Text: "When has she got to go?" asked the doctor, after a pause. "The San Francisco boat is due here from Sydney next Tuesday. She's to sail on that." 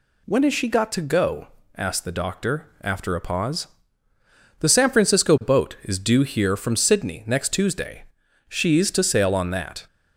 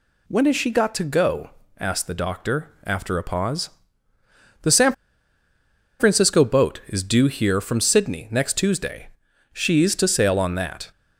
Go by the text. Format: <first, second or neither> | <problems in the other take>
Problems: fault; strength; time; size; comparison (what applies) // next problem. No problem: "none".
first | pauses between "San" and "Francisco"; at 4.9 s; 1.0 s long